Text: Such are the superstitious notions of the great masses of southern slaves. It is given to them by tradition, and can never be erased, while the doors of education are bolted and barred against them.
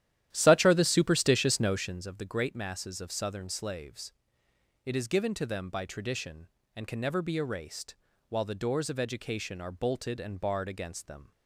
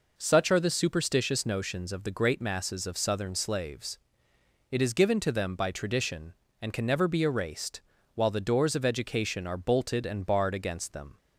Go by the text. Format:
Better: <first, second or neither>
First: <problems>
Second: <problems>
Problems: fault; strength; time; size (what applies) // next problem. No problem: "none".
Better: second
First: starts louder than the rest; strong; until 2.1 s; 12 dB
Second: none